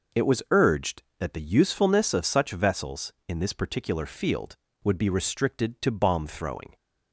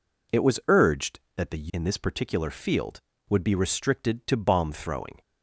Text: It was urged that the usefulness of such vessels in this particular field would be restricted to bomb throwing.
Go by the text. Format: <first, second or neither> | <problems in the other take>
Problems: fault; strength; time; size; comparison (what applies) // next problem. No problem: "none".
first | skips "usefulness of such vessels"; at 1.7 s